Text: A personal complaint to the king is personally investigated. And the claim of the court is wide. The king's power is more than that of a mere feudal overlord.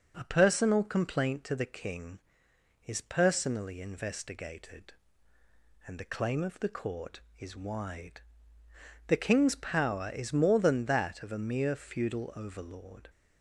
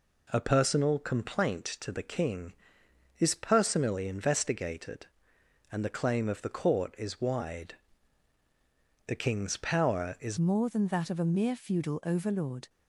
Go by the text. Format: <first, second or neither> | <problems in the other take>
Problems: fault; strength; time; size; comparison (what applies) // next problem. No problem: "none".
first | changes voice at "more"; from 10.3 s on; 2.3 s long